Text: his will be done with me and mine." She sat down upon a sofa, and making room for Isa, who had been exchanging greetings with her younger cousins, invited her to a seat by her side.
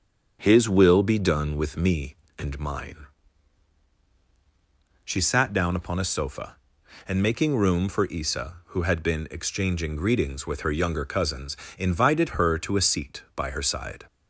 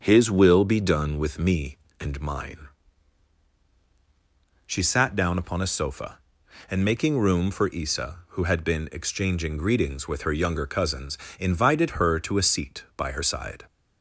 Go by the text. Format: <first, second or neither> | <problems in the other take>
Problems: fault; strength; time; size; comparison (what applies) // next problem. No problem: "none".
neither | starts louder than the rest; the same in both